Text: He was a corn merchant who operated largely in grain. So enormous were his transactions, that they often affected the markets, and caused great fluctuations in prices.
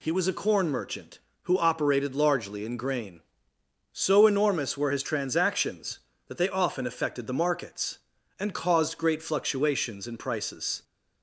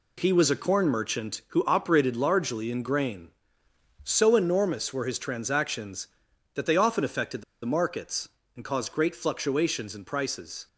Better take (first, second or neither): first